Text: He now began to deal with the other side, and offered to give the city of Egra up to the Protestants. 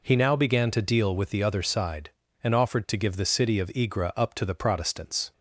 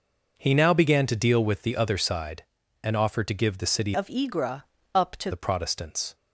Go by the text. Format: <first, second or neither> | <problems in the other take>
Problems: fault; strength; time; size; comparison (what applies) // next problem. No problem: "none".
first | changes voice from "of" to "to"; from 3.9 to 5.3 s; 1.4 s long // pauses between "Egra" and "up"; slight; at 4.6 s; 0.30 s long